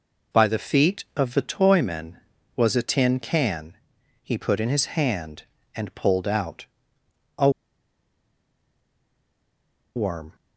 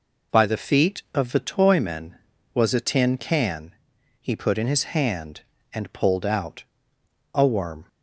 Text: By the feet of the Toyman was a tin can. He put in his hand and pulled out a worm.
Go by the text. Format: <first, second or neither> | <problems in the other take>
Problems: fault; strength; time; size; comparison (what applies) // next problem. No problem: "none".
second | pauses between "out" and "a"; noticeable; at 6.6 s; 0.72 s long; noticeable in the second // pauses between "a" and "worm"; strong; at 7.4 s; 2.4 s long